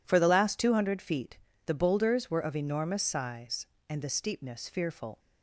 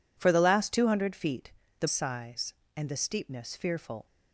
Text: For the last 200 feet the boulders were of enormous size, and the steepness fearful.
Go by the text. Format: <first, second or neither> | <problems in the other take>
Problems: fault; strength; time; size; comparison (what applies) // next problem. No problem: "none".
first | pauses between "feet" and "the"; slight; at 1.5 s; 0.26 s long; slight in the first // skips "boulders were of enormous"; at 1.8 s